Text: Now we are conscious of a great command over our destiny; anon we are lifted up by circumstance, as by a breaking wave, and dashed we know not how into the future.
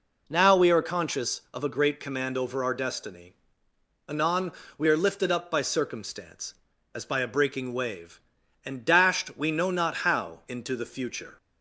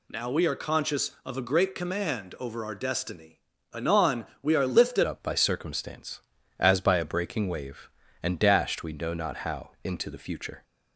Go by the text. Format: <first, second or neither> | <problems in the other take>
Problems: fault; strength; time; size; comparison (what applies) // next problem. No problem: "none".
first | pauses between "anon" and "we"; slight; at 4.2 s; 0.16 s long; slight in the first // changes voice at "up"; from 5.0 s on; 5.6 s long // pauses between "how" and "into"; slight; at 9.6 s; 0.16 s long